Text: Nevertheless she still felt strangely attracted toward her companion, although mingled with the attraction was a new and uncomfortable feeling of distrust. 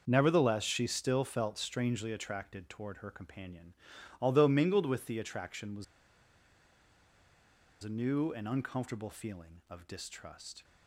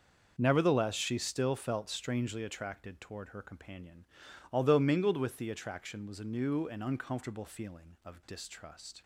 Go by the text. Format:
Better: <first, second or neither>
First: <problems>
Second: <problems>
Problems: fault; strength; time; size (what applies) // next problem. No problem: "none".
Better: second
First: starts louder than the rest; until 1.0 s; 6.5 dB // pauses between "was" and "a"; strong; at 5.8 s; 1.9 s long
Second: starts louder than the rest; until 1.3 s; 6.5 dB